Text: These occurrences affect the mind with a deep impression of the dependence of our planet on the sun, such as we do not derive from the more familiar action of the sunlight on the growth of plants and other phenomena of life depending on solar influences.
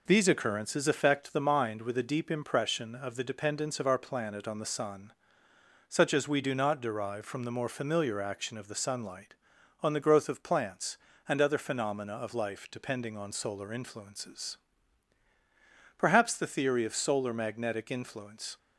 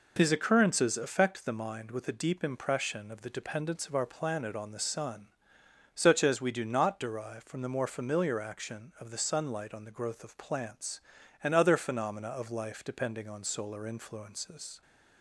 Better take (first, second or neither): second